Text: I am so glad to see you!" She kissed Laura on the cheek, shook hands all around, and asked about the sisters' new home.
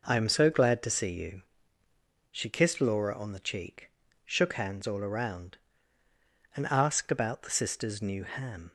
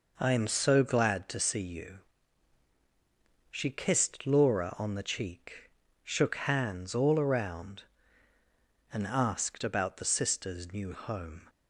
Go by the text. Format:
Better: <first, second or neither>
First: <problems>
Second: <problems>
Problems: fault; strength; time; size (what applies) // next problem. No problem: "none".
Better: second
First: says "ham" for "home"; at 8.2 s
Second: none